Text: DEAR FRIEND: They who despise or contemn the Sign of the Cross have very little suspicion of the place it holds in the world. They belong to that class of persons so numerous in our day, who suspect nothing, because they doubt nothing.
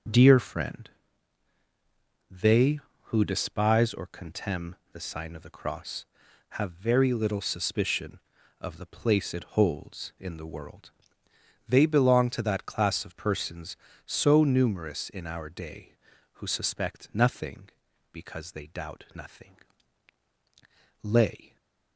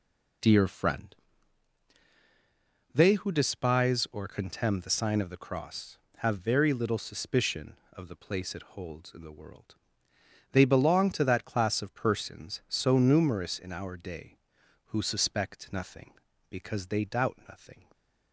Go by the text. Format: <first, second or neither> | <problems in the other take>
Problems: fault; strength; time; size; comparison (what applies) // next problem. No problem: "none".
second | starts louder than the rest; until 2.4 s; 6.5 dB // pauses between "contemn" and "the"; slight; at 4.7 s; 0.16 s long // goes on to say "Lay"; from 21.0 s on; 0.54 s long // stays silent after the last word; slight; from 21.4 s on; 0.5 s long